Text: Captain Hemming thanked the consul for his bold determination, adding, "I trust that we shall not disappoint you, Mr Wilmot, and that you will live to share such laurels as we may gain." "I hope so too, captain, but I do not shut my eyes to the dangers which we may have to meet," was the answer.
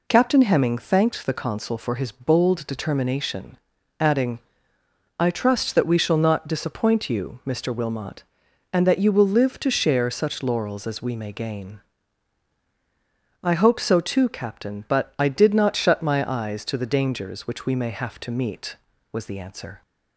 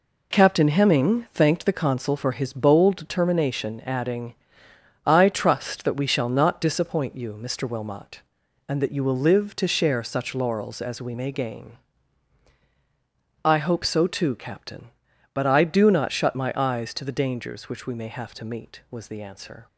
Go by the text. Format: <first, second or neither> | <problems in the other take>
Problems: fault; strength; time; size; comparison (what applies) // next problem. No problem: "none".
second | says "did" for "do"; at 15.2 s